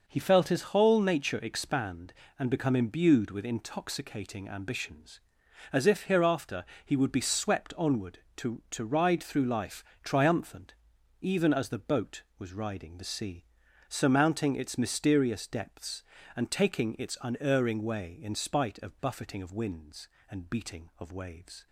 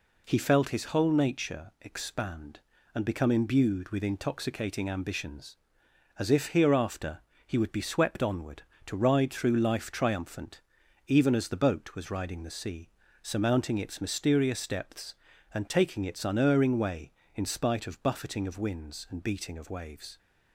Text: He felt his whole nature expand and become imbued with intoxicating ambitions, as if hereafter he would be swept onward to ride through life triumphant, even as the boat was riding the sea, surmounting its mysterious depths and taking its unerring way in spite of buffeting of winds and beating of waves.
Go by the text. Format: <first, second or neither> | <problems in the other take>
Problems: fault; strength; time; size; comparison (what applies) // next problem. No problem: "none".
second | pauses between "hereafter" and "he"; slight; at 6.6 s; 0.20 s long; slight in the second // says "to" twice; at 8.7 s // pauses between "life" and "triumphant"; slight; at 9.8 s; 0.22 s long